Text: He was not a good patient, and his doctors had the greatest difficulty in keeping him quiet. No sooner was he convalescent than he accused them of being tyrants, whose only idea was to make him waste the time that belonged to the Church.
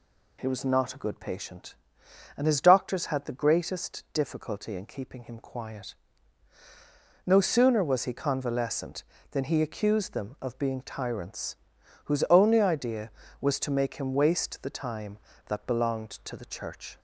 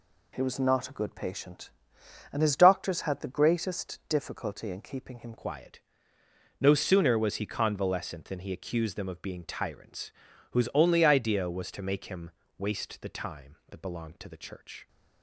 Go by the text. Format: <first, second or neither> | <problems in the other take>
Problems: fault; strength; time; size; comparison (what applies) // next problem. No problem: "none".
first | changes voice at "quiet"; from 5.3 s on; 9.5 s long // pauses between "him" and "waste"; slight; at 12.3 s; 0.26 s long